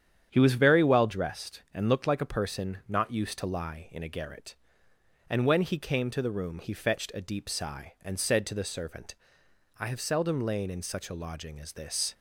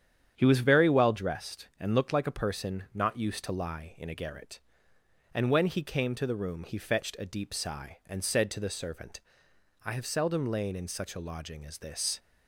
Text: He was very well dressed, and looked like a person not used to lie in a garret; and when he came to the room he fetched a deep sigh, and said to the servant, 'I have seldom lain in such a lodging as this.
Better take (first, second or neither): neither